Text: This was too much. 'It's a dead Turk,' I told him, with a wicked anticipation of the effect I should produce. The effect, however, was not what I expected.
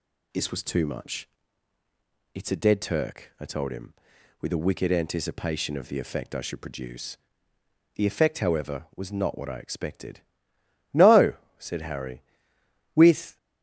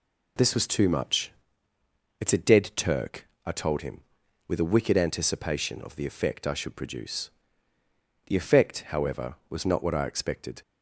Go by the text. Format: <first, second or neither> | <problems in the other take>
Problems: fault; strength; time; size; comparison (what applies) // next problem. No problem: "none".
second | goes on to say "No said Harry with"; strong; from 10.9 s on; 2.4 s long